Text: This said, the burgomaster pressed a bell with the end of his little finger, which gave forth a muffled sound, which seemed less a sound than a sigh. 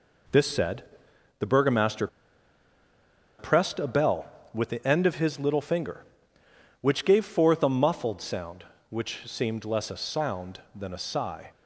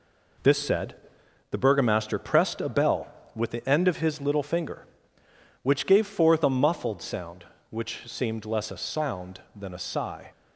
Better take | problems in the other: second | pauses between "burgomaster" and "pressed"; strong; at 2.0 s; 1.3 s long

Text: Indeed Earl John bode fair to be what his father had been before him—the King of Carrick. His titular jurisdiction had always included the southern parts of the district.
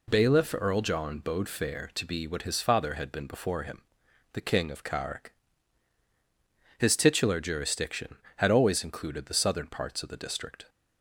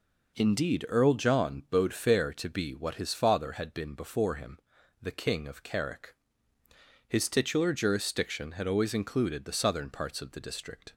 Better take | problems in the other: second | says "Bailiff" for "Indeed"; at 0.0 s

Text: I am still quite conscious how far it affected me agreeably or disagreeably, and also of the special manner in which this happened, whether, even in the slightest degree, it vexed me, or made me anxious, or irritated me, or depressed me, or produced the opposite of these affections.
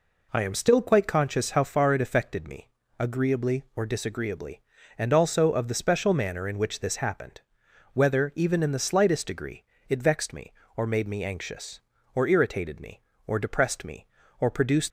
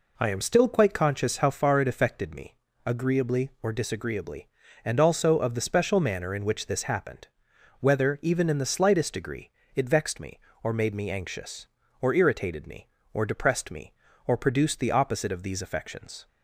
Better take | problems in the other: second | pauses between "me" and "agreeably"; slight; at 2.6 s; 0.32 s long; slight in the second // stops before "the opposite of these affections"; at 14.8 s

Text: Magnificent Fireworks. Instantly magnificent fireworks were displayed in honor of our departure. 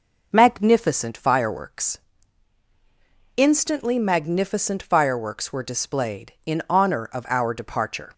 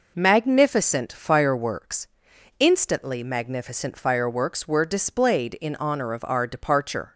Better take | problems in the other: neither | none

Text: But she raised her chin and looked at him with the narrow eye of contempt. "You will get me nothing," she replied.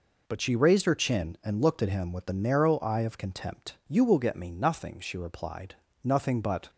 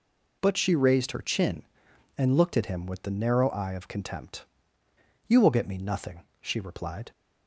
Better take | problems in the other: second | goes on to say "Nothing but"; noticeable; from 6.0 s on; 0.68 s long

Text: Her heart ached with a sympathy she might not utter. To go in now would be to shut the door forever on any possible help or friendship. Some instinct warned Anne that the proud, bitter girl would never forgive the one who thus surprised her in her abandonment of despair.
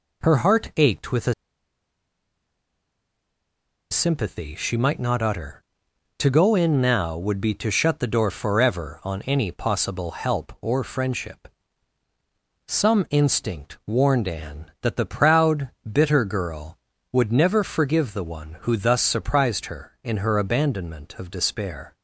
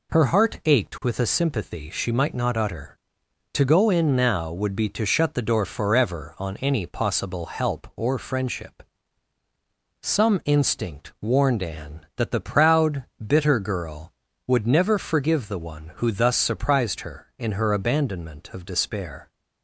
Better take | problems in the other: second | pauses between "a" and "sympathy"; strong; at 1.3 s; 2.5 s long

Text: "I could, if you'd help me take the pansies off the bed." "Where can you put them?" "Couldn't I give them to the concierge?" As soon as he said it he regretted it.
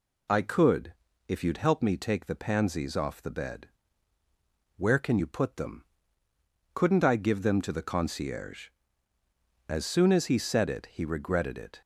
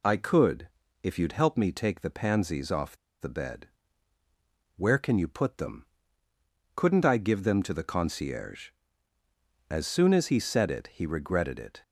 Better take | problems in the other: first | pauses between "off" and "the"; slight; at 2.9 s; 0.23 s long

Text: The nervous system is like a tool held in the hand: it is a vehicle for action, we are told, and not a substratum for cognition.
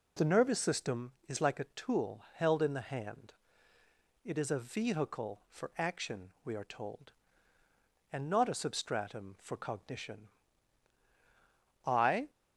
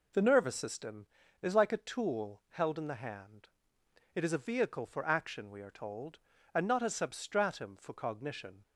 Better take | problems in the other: second | goes on to say "I"; slight; from 11.8 s on; 0.44 s long

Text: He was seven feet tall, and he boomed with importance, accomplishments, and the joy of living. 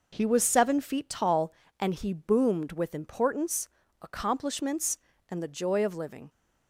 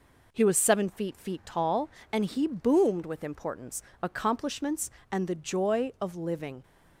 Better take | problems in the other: first | says "feet" twice; at 1.1 s

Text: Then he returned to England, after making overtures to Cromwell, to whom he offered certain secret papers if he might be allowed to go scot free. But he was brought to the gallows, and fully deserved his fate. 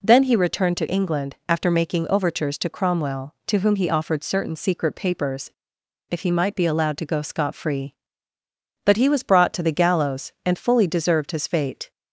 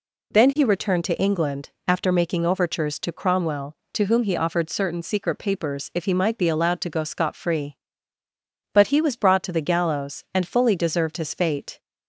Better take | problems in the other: second | pauses between "papers" and "if"; noticeable; at 5.5 s; 0.60 s long

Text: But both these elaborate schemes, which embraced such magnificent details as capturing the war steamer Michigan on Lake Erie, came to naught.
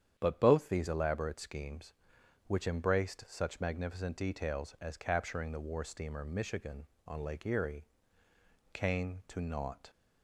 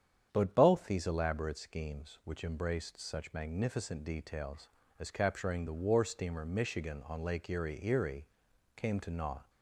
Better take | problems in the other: first | starts louder than the rest; strong; until 1.3 s; 8.5 dB; strong in the first // says "Erie" twice; at 7.8 s

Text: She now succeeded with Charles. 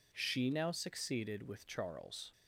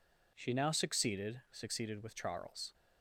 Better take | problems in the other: first | says "succeeded" twice; at 1.5 s

